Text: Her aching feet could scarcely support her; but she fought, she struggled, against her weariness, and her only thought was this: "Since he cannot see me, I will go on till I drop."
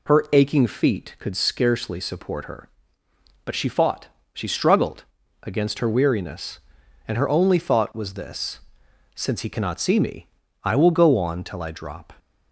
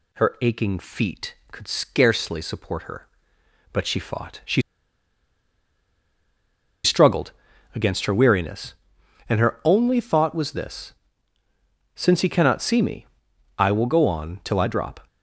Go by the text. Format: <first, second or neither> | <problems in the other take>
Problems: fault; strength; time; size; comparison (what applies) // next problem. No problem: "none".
first | pauses between "she" and "struggled"; strong; at 4.6 s; 2.2 s long